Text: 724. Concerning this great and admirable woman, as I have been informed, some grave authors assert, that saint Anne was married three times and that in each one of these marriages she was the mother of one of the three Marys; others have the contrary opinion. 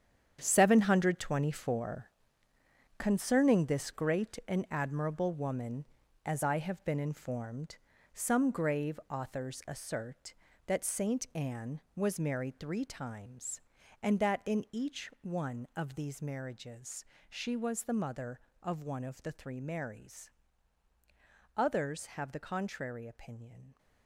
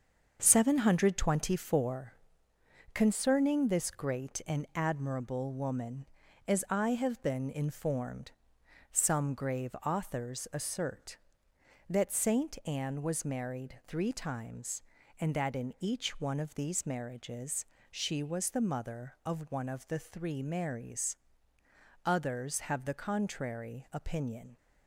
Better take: second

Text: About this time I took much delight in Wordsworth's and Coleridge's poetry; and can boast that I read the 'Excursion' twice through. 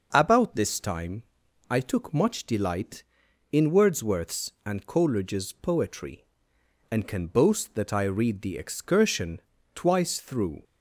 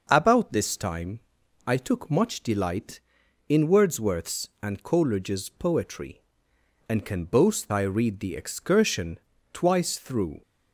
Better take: first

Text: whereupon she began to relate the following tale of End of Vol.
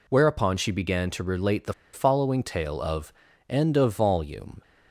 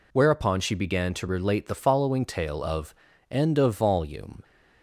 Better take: second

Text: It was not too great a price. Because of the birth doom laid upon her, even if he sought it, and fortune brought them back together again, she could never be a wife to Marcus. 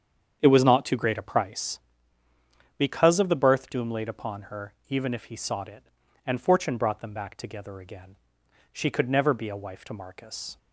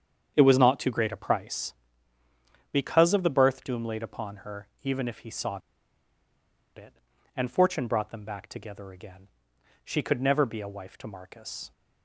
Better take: first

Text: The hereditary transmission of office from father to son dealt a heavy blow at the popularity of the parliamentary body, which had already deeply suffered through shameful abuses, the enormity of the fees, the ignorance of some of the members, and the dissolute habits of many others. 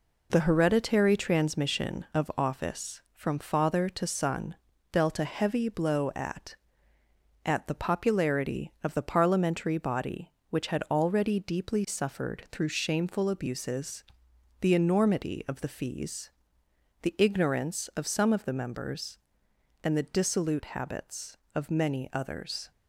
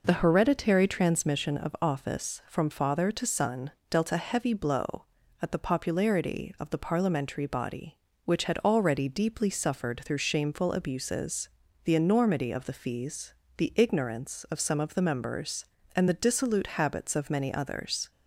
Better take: second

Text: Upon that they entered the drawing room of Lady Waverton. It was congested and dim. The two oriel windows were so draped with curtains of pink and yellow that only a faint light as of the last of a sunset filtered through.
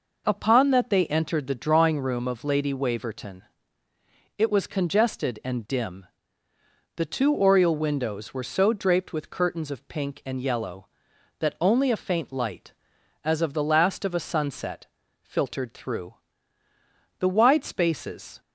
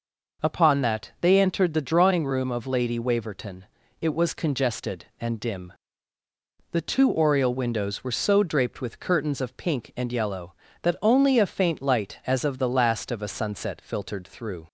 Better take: second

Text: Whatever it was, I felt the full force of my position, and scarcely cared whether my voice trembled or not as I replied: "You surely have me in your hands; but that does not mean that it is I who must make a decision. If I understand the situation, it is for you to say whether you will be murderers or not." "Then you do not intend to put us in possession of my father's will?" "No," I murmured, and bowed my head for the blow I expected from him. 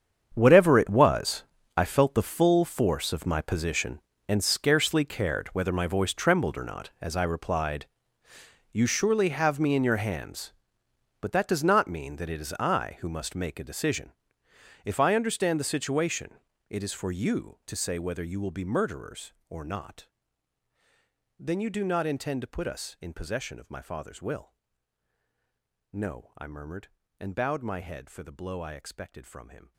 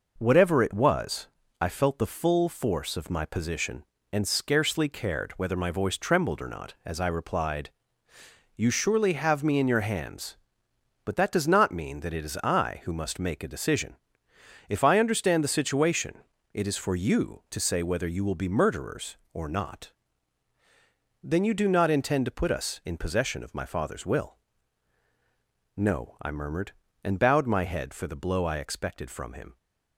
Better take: second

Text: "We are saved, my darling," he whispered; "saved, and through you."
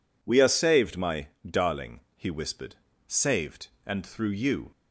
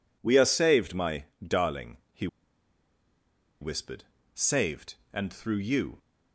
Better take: first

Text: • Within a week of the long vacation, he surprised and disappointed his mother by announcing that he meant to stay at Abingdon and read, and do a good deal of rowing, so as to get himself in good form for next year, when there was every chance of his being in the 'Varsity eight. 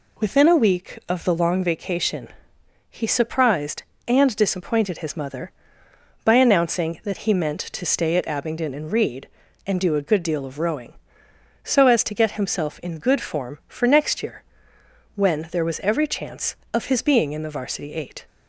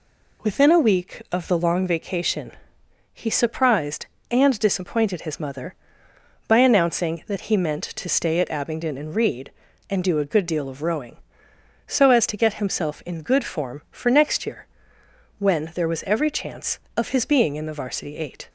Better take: neither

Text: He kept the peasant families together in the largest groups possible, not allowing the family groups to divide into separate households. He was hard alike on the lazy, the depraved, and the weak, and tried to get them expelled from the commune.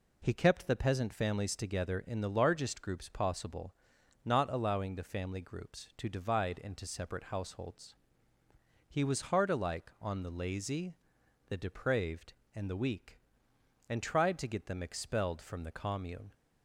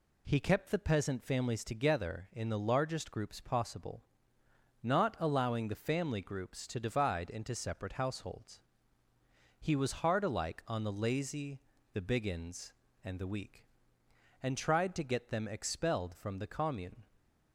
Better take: first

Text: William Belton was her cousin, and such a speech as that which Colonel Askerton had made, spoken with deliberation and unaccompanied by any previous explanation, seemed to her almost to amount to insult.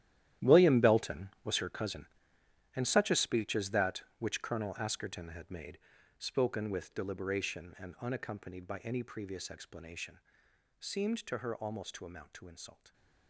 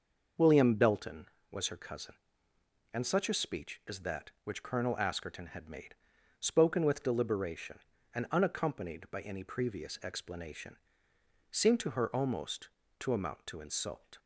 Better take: second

